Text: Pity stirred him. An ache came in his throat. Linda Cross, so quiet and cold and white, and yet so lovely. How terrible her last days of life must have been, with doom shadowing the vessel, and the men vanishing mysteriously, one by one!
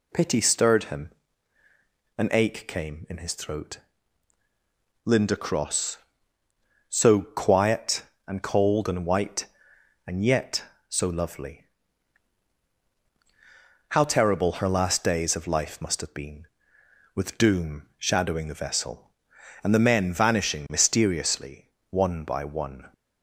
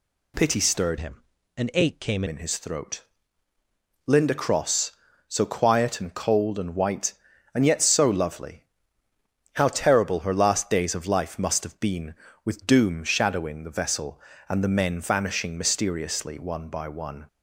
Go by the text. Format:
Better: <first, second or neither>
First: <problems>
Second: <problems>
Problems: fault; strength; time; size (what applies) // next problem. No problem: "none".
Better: first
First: none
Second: changes voice from "him" to "came"; from 0.9 to 2.2 s; 1.3 s long